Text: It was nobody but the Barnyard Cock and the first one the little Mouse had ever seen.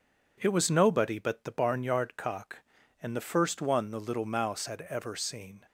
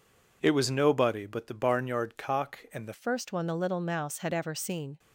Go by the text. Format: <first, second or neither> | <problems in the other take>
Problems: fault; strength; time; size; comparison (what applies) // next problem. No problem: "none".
first | changes voice at "first"; from 2.9 s on; 2.0 s long